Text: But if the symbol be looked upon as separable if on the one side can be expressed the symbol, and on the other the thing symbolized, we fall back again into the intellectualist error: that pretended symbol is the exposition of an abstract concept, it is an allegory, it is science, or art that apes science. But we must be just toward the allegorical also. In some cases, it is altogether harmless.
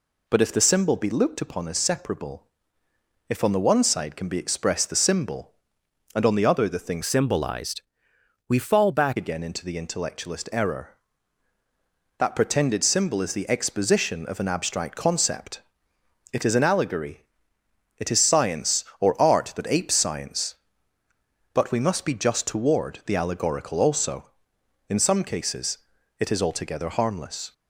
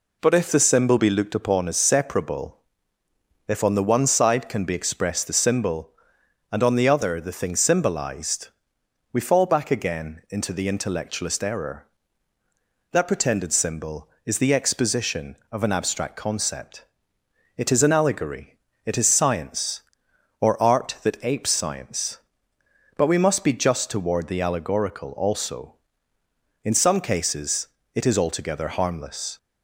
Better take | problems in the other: second | pauses between "separable" and "if"; noticeable; at 2.4 s; 0.86 s long; noticeable in the second // changes voice from "symbolized" to "back"; from 7.0 to 9.1 s; 2.1 s long

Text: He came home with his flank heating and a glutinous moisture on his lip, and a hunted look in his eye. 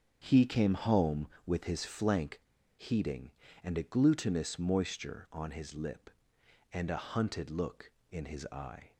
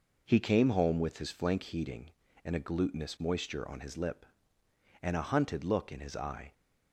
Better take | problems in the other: second | starts louder than the rest; strong; until 1.2 s; 7.5 dB // pauses between "flank" and "heating"; at 2.4 s; 0.37 s long

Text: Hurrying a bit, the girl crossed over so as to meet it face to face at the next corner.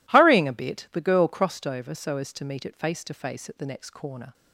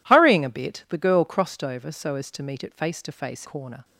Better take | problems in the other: first | skips "at the next"; at 3.4 s

